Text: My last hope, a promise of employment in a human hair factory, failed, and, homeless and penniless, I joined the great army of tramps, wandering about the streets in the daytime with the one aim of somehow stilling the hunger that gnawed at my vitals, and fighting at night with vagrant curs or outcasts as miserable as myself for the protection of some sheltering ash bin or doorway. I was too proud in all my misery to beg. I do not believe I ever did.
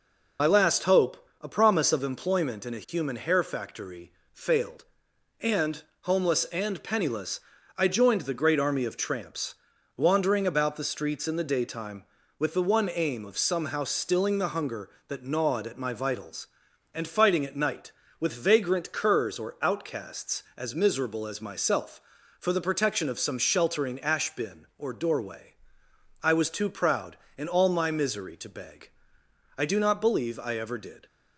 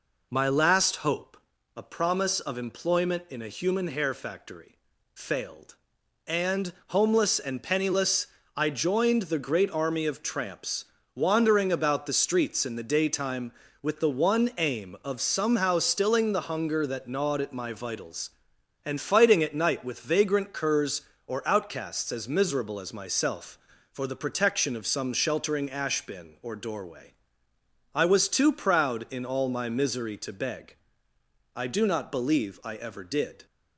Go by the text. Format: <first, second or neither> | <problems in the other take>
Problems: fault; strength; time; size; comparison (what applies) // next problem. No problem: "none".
second | loses the start of "My"; at 0.3 s; 45 ms